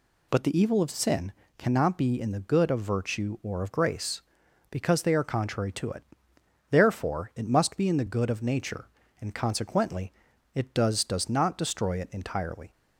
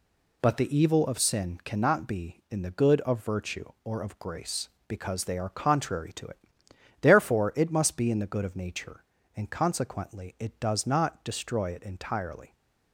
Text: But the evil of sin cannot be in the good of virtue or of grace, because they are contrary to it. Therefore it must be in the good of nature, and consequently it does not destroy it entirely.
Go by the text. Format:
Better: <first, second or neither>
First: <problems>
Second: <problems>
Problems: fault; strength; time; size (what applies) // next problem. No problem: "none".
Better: second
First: pauses between "sin" and "cannot"; slight; at 1.3 s; 0.26 s long // pauses between "consequently" and "it"; at 10.1 s; 0.42 s long // says "does" twice; at 11.0 s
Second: none